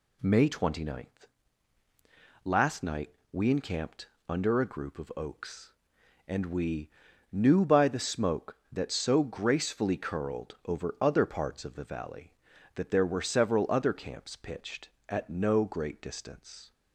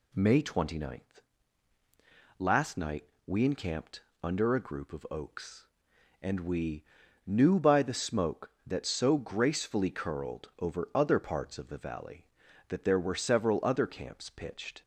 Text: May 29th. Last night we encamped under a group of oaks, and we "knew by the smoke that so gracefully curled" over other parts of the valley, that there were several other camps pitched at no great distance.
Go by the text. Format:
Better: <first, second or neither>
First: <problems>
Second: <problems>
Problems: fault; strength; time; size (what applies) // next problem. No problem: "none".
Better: first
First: pauses between "night" and "we"; slight; at 3.1 s; 0.20 s long // pauses between "encamped" and "under"; slight; at 4.0 s; 0.20 s long // pauses between "we" and "knew"; at 6.9 s; 0.40 s long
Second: pauses between "night" and "we"; slight; at 3.0 s; 0.20 s long // pauses between "encamped" and "under"; slight; at 4.0 s; 0.20 s long // pauses between "we" and "knew"; at 6.8 s; 0.40 s long // stops before "at no great distance"; at 14.8 s